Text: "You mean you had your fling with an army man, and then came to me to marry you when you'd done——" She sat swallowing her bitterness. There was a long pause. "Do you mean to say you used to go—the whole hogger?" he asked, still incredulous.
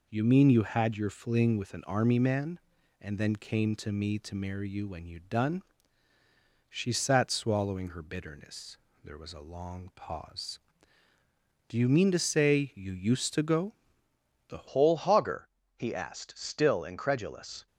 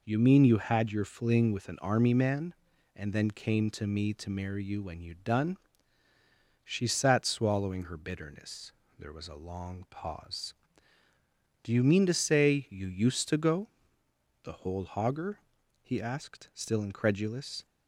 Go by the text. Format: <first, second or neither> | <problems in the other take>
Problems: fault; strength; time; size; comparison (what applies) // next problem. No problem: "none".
second | changes voice at "whole"; from 14.6 s on; 3.0 s long